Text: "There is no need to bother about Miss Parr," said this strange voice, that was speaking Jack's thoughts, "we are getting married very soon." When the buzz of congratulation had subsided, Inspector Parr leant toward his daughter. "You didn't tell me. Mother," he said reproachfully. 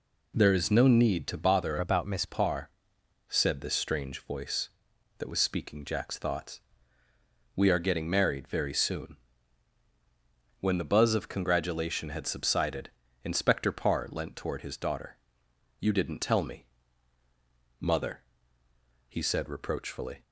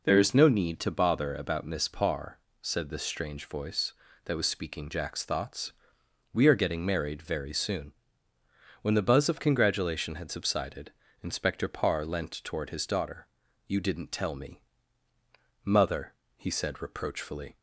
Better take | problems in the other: second | changes voice from "about" to "Miss"; from 1.7 to 2.2 s; 0.5 s long

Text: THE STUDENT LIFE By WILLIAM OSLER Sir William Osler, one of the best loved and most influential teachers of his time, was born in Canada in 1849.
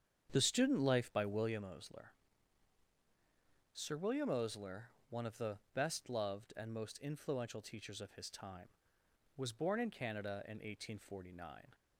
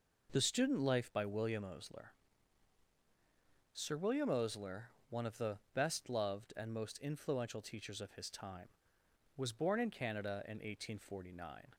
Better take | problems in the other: second | starts louder than the rest; strong; until 1.6 s; 8 dB // pauses between "OSLER" and "Sir"; strong; at 2.1 s; 1.6 s long; strong in the second // pauses between "the" and "best"; slight; at 5.5 s; 0.16 s long; slight in the second

